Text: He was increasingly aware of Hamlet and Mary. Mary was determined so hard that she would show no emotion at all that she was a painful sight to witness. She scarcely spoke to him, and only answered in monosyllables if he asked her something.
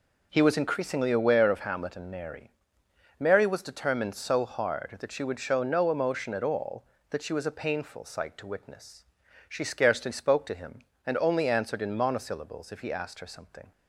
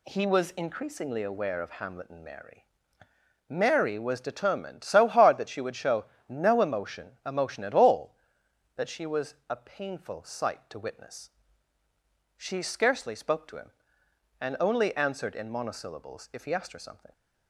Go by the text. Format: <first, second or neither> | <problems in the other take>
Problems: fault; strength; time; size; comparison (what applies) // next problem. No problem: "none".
first | pauses between "show" and "no"; slight; at 6.0 s; 0.24 s long // says "emotion" twice; at 7.2 s